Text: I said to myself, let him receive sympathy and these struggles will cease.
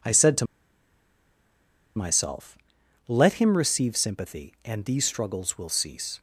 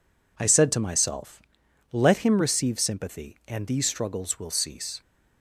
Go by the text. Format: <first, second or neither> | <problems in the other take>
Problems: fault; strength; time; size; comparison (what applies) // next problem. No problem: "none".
second | pauses between "to" and "myself"; strong; at 0.4 s; 1.5 s long